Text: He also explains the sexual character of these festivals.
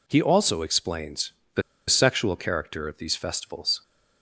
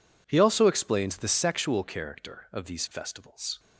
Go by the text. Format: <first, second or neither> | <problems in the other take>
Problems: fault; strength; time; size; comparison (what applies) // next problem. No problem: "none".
second | pauses between "explains" and "the"; slight; at 1.3 s; 0.24 s long // pauses between "the" and "sexual"; slight; at 1.6 s; 0.28 s long